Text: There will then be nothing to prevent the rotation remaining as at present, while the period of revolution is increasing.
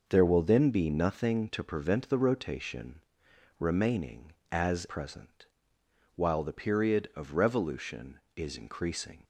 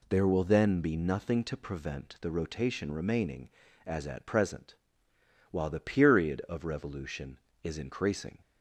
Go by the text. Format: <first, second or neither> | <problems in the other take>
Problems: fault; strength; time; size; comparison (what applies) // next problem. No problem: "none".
second | pauses between "rotation" and "remaining"; noticeable; at 3.0 s; 0.58 s long // skips "at"; at 4.8 s